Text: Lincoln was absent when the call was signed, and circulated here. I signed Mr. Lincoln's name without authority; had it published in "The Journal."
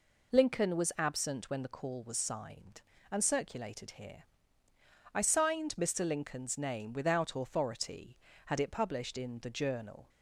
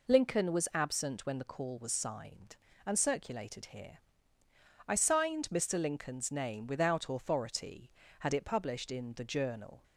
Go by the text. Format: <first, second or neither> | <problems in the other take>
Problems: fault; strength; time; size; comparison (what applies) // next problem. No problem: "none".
neither | none